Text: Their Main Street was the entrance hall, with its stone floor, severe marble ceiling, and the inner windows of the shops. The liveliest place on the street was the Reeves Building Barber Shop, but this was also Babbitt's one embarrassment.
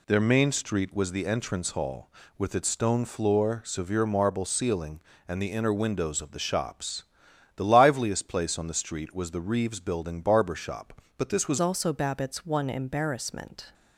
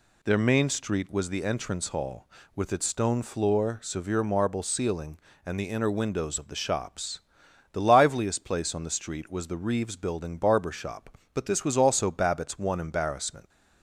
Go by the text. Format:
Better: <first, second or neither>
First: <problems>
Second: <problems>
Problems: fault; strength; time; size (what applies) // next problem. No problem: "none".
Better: second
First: changes voice at "also"; from 11.5 s on; 2.2 s long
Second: none